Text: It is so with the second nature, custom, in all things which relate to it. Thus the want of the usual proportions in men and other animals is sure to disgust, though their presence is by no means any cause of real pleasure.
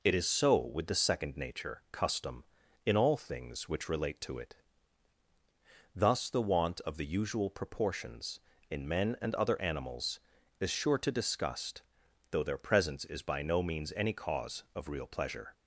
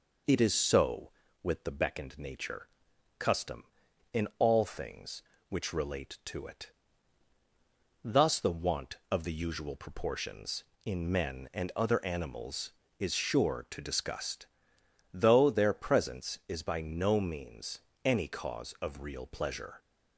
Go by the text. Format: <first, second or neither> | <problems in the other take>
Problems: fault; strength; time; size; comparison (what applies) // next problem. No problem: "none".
first | says "beckoned" for "second"; at 1.7 s // pauses between "means" and "any"; slight; at 17.8 s; 0.22 s long